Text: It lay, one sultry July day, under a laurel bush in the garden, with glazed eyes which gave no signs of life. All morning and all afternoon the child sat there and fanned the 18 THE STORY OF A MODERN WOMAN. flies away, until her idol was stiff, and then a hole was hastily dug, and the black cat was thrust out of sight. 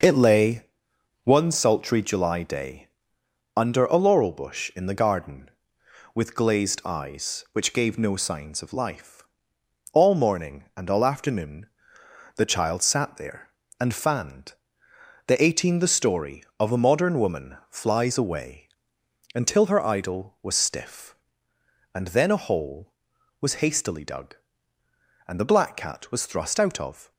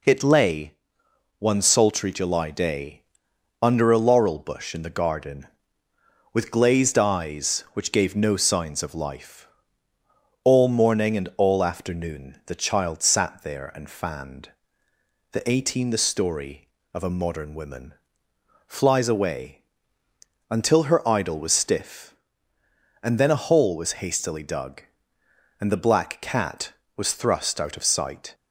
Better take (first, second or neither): second